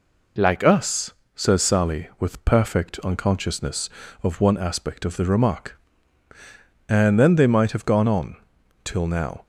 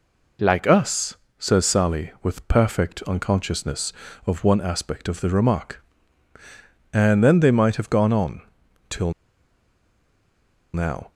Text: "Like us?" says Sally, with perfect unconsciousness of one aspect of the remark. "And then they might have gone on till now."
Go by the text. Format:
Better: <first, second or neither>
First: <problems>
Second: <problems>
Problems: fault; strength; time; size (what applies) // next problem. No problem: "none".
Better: first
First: pauses between "on" and "till"; noticeable; at 8.3 s; 0.48 s long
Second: pauses between "on" and "till"; noticeable; at 8.4 s; 0.48 s long // pauses between "till" and "now"; strong; at 9.1 s; 1.6 s long